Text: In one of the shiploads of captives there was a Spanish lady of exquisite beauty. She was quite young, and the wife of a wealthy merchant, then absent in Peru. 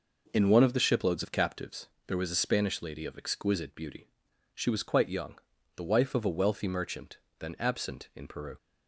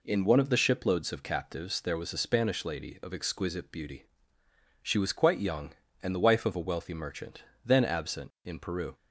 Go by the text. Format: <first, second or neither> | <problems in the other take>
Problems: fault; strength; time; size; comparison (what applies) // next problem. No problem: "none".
second | pauses between "captives" and "there"; slight; at 1.8 s; 0.20 s long // skips "and"; at 5.5 s